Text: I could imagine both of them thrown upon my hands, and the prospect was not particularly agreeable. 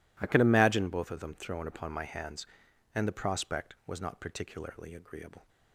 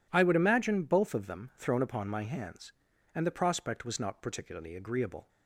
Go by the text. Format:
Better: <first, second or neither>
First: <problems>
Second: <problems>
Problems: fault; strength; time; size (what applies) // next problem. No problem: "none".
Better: first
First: none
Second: says "would" for "could"; at 0.2 s